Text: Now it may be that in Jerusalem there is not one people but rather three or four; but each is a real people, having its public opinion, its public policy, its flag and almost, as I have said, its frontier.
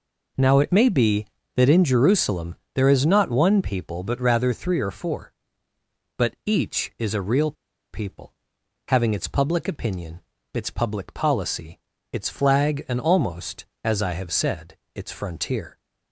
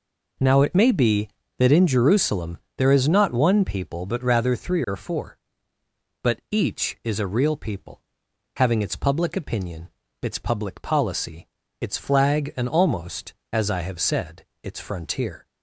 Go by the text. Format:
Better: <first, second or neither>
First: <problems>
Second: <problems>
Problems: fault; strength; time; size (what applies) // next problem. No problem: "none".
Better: second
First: pauses between "Jerusalem" and "there"; slight; at 2.5 s; 0.18 s long // pauses between "real" and "people"; at 7.5 s; 0.39 s long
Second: pauses between "Jerusalem" and "there"; slight; at 2.5 s; 0.18 s long